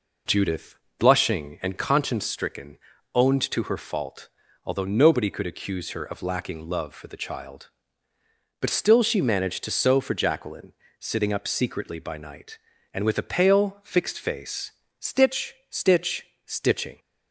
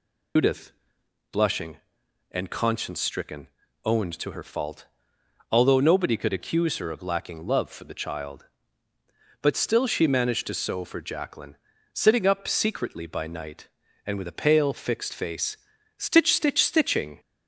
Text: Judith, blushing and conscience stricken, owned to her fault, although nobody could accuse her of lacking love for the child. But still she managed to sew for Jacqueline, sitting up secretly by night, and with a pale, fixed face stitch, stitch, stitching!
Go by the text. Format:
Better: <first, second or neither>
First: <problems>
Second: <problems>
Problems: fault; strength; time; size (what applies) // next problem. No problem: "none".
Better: first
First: pauses between "face" and "stitch"; slight; at 14.7 s; 0.26 s long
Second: loses the start of "Judith"; at 0.3 s; 115 ms // pauses between "face" and "stitch"; at 15.5 s; 0.42 s long